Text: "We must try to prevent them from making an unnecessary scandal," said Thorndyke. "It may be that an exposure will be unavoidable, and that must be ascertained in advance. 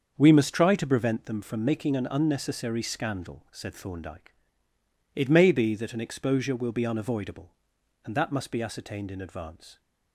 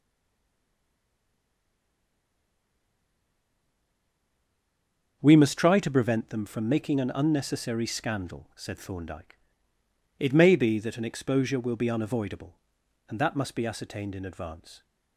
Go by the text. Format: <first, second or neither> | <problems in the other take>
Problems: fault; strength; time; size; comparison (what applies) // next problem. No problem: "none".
first | stays silent before the first word; strong; until 5.2 s; 5.2 s long // starts louder than the rest; until 6.2 s; 7 dB; also in the first